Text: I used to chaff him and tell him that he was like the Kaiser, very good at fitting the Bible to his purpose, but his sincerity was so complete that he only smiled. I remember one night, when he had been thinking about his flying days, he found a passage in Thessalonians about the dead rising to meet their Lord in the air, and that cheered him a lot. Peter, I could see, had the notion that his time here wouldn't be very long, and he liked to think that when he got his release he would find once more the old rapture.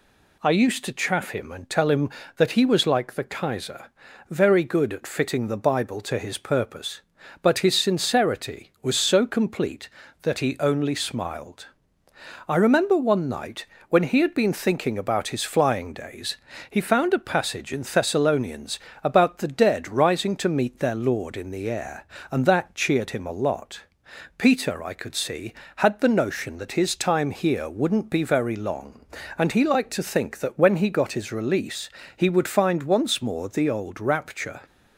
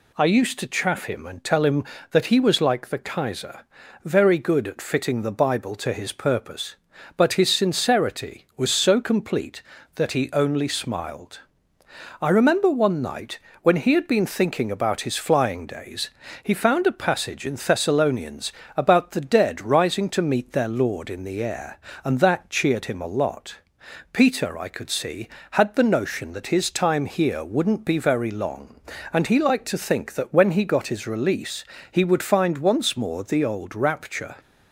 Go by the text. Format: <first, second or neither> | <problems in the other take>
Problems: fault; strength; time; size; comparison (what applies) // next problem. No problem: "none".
neither | pauses between "Thessalonians" and "about"; slight; the same in both // pauses between "release" and "he"; slight; the same in both